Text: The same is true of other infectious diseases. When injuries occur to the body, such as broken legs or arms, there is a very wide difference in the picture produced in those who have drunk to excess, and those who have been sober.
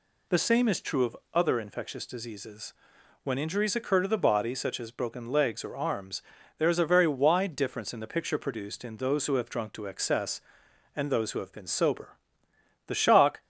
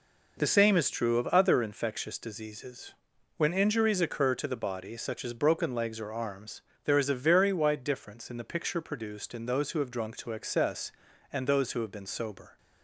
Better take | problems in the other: second | pauses between "of" and "other"; slight; at 1.1 s; 0.18 s long // goes on to say "The shock"; from 12.8 s on; 0.54 s long

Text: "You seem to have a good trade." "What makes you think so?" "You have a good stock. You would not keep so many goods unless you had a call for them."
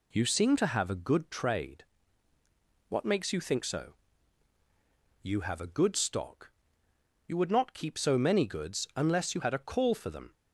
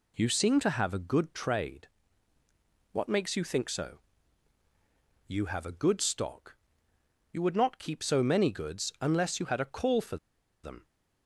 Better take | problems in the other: first | pauses between "for" and "them"; noticeable; at 10.1 s; 0.47 s long

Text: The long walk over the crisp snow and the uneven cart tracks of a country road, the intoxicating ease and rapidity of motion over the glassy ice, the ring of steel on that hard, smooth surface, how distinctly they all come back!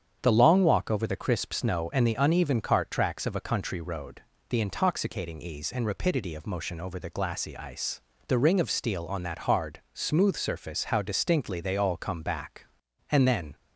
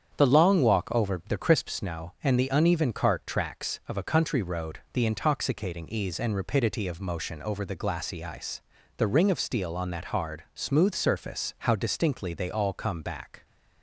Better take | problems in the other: second | starts louder than the rest; strong; until 1.2 s; 8 dB; strong in the second // goes on to say "And then"; slight; from 13.0 s on; 0.46 s long

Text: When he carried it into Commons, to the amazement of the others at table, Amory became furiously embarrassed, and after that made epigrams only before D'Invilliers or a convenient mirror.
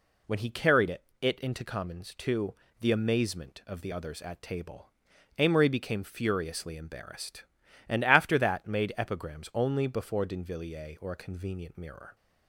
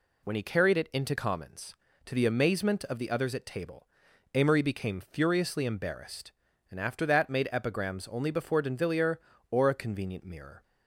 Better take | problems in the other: second | says "it" twice; at 1.2 s // pauses between "to" and "the"; slight; at 2.5 s; 0.28 s long

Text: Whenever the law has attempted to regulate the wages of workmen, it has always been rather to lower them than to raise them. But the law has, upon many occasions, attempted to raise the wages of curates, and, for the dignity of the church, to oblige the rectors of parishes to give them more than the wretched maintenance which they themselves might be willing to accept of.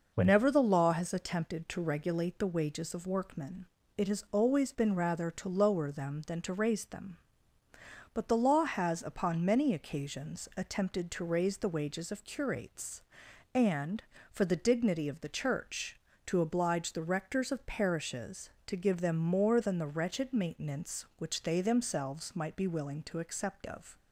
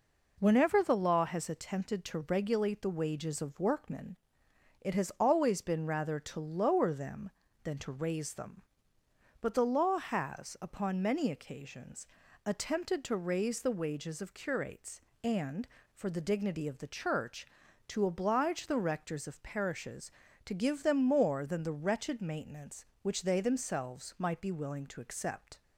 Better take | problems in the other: first | stops before "of"; at 25.6 s

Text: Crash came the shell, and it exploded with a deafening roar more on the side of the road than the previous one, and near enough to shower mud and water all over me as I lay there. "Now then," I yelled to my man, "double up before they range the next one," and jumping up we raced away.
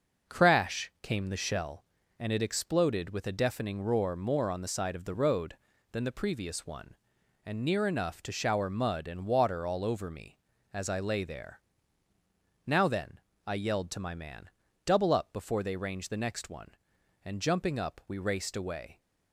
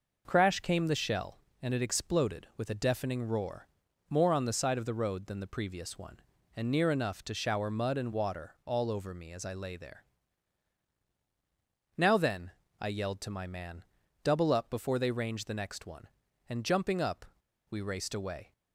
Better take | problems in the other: first | pauses between "roar" and "more"; at 3.6 s; 0.40 s long // pauses between "up" and "we"; noticeable; at 17.2 s; 0.45 s long

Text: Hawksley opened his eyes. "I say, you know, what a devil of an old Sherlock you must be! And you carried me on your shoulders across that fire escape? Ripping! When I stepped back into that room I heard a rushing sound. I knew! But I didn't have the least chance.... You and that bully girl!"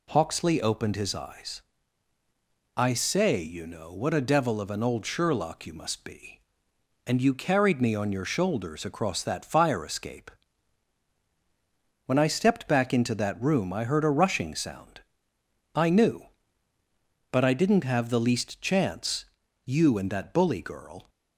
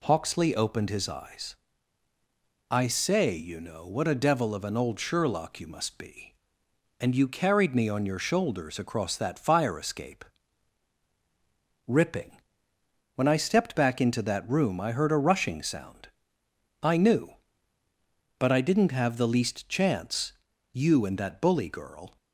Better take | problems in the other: second | skips "Ripping"; at 11.1 s

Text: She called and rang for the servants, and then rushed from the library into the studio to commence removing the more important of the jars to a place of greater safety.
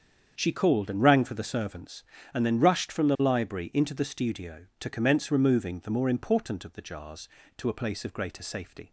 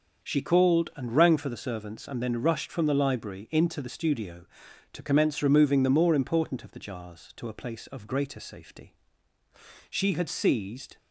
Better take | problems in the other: first | starts louder than the rest; until 1.3 s; 6.5 dB; strong in the first // goes on to say "She had seized"; noticeable; from 9.8 s on; 1.0 s long

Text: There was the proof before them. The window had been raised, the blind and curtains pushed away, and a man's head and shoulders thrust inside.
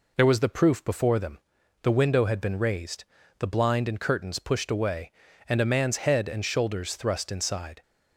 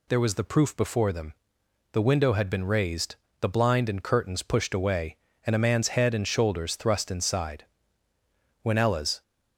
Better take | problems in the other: first | goes on to say "When Ella's"; from 8.6 s on; 0.60 s long

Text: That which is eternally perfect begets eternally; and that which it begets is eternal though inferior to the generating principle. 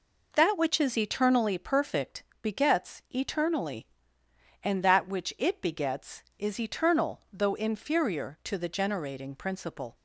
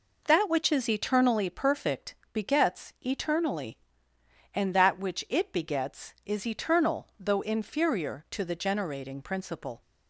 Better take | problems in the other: neither | pauses between "perfect" and "begets"; slight; the same in both

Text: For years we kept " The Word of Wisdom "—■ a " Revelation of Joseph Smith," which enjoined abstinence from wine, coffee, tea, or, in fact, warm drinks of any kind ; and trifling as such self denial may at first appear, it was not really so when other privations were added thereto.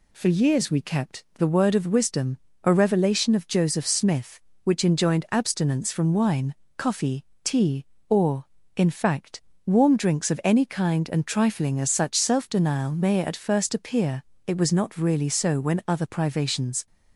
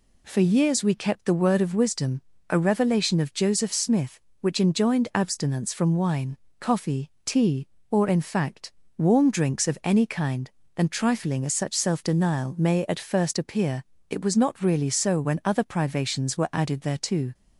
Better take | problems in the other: second | stops before "were added thereto"; at 16.8 s

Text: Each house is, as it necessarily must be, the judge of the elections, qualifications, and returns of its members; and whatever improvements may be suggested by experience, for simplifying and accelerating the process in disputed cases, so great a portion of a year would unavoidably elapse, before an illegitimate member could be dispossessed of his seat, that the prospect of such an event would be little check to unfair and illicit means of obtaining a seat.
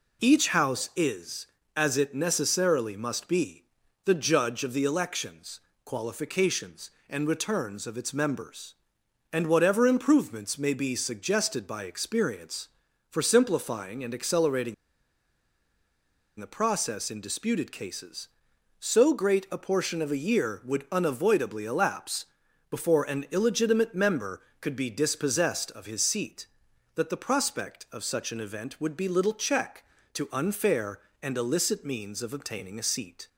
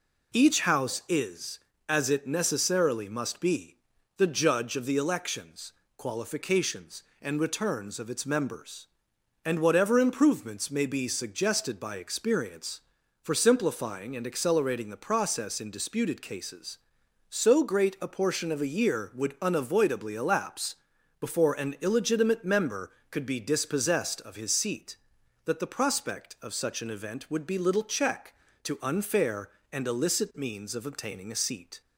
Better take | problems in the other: second | pauses between "accelerating" and "the"; strong; at 14.7 s; 1.6 s long

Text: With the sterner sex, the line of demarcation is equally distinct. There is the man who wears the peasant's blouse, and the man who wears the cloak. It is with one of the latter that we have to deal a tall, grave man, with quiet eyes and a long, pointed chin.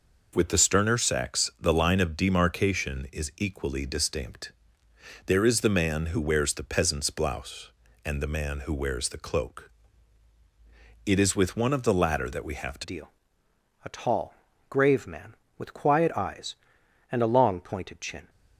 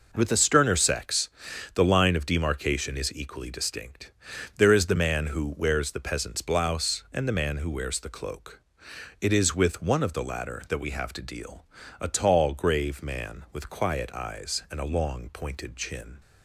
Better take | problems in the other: second | changes voice at "deal"; from 12.8 s on; 5.4 s long // pauses between "deal" and "a"; noticeable; at 13.1 s; 0.74 s long; slight in the second

